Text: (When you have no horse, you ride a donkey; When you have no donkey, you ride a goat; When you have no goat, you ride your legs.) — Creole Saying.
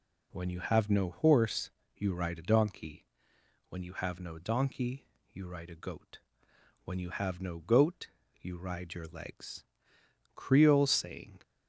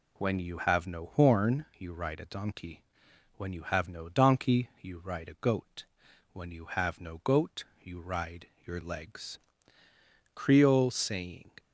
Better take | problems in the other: first | says "horn" for "horse"; at 1.0 s // pauses between "ride" and "your"; slight; at 8.4 s; 0.18 s long

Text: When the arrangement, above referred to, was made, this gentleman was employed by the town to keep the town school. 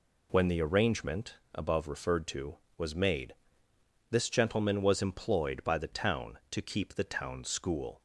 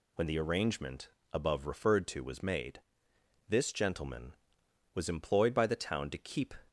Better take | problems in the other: first | stops before "the town school"; at 6.6 s

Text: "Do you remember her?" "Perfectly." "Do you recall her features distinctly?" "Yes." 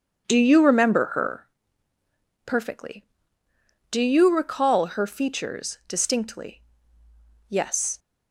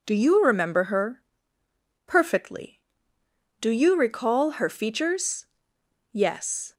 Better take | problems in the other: first | skips "distinctly"; at 5.7 s

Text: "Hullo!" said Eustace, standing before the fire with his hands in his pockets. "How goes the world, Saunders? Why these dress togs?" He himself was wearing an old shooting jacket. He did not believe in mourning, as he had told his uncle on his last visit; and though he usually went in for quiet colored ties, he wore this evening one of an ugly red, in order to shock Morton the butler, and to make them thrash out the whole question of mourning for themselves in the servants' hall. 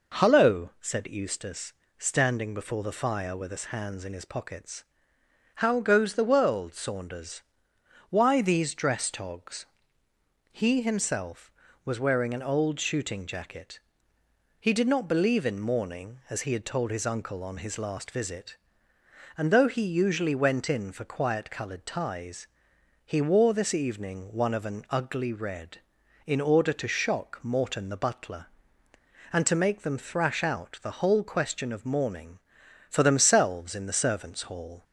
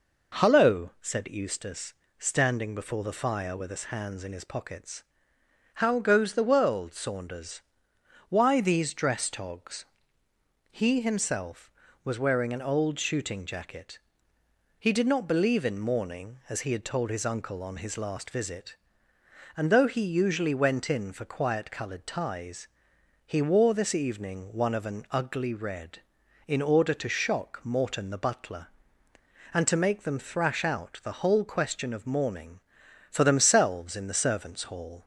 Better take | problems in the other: neither | none

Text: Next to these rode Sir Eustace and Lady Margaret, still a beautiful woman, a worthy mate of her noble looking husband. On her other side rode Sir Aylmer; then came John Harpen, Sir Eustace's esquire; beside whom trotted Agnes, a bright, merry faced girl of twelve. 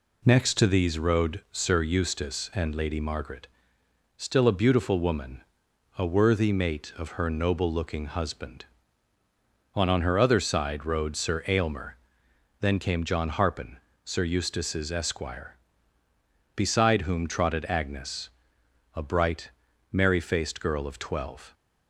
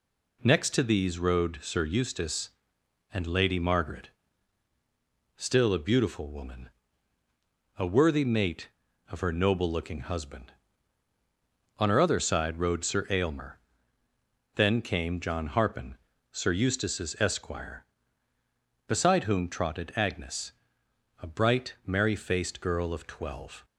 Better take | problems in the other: second | says "On" twice; at 9.8 s

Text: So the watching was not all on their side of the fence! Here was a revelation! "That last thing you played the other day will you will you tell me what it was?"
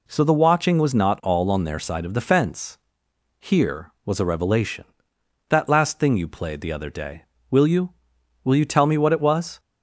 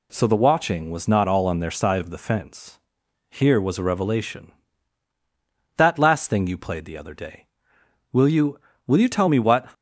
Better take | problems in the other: first | stops before "it was"; at 9.7 s

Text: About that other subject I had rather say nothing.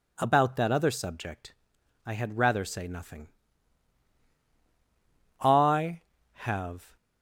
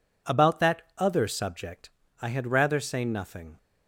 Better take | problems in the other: second | pauses between "subject" and "I"; noticeable; at 1.5 s; 0.52 s long; slight in the second // goes on to say "I have"; from 5.4 s on; 1.5 s long

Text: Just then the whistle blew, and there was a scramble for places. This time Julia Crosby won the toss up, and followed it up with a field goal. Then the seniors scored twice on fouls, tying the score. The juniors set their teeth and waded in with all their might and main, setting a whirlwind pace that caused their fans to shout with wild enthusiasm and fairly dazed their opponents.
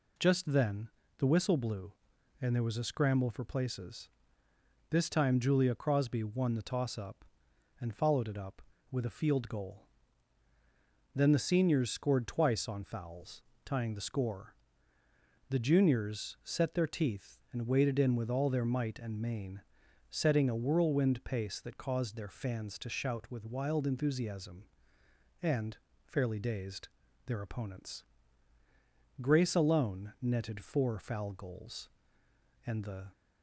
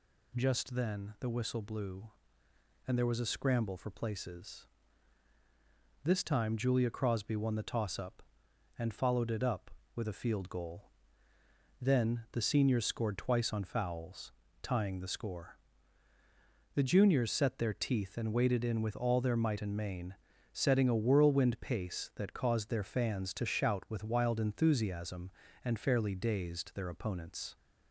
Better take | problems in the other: second | pauses between "then" and "the"; slight; at 0.8 s; 0.30 s long // pauses between "and" and "fairly"; slight; at 25.7 s; 0.30 s long // pauses between "dazed" and "their"; at 26.8 s; 0.37 s long // goes on to say "Grace alone netted four foul goals and the"; strong; from 29.1 s on; 3.8 s long

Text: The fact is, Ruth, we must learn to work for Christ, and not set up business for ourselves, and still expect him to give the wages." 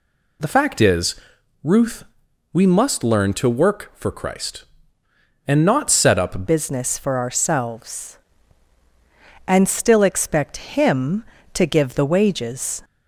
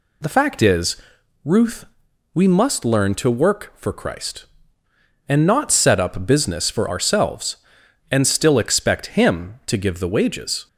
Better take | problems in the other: second | changes voice at "business"; from 6.4 s on; 6.4 s long

